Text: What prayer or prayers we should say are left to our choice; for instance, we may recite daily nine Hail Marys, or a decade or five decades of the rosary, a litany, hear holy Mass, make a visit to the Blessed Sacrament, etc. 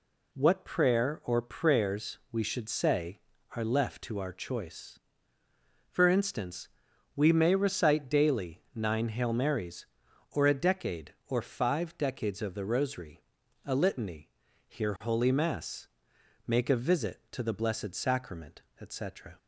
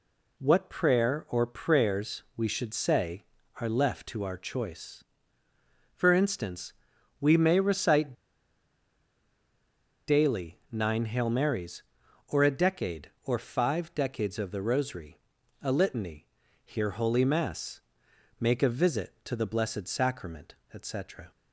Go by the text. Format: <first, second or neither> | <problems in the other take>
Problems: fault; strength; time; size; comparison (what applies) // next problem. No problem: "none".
first | pauses between "recite" and "daily"; strong; at 8.1 s; 1.9 s long